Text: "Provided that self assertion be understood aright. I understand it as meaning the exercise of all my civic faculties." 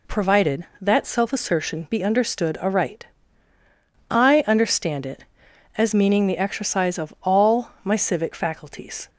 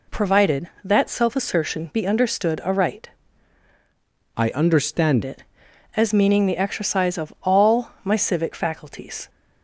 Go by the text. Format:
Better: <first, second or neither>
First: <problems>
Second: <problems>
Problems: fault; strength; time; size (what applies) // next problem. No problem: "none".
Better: first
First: none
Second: changes voice from "I" to "understand"; from 4.3 to 5.2 s; 0.9 s long